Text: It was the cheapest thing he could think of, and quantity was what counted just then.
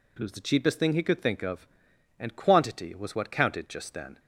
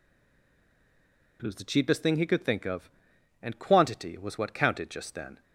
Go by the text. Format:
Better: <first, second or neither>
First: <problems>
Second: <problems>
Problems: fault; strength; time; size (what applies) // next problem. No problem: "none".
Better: first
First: none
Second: stays silent before the first word; noticeable; until 1.3 s; 1.3 s long